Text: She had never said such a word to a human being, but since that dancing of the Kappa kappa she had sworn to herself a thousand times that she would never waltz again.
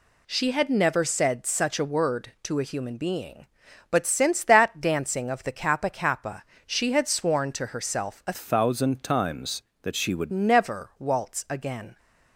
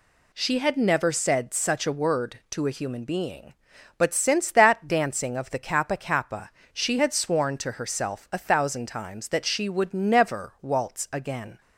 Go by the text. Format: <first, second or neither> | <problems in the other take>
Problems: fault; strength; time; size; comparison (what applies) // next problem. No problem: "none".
second | pauses between "kappa" and "she"; slight; at 6.4 s; 0.22 s long; slight in the second // changes voice from "thousand" to "would"; from 8.3 to 10.3 s; 2.0 s long